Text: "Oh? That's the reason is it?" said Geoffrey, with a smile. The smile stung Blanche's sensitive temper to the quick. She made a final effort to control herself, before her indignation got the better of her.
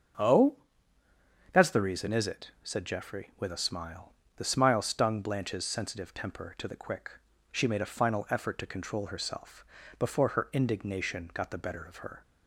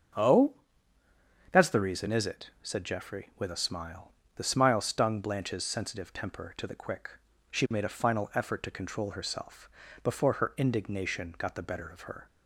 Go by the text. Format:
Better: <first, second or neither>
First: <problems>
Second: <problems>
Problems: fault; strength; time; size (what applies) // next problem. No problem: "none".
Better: neither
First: starts louder than the rest; until 2.1 s; 6.5 dB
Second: starts louder than the rest; until 2.1 s; 6.5 dB